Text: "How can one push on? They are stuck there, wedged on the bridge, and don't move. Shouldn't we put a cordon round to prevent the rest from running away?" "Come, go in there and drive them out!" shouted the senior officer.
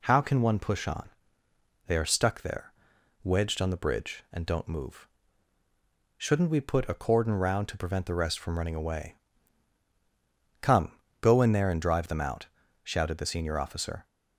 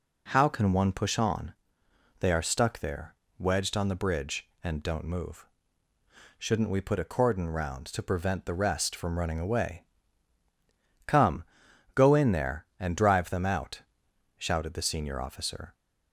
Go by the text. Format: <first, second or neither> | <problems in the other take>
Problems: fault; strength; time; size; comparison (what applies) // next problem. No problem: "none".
neither | none